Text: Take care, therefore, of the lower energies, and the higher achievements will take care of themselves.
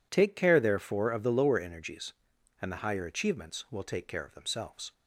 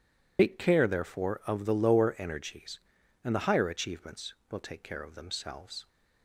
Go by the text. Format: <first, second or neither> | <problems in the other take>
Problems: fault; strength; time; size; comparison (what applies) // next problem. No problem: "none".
first | loses the start of "Take"; at 0.3 s; 100 ms